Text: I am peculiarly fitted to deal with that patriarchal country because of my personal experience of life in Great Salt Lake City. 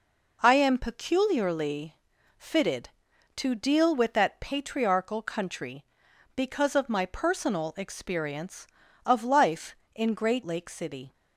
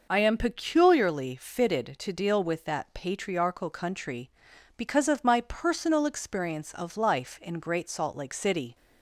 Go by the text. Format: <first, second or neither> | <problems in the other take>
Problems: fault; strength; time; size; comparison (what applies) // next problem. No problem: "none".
second | pauses between "peculiarly" and "fitted"; at 1.9 s; 0.40 s long // skips "Salt"; at 10.4 s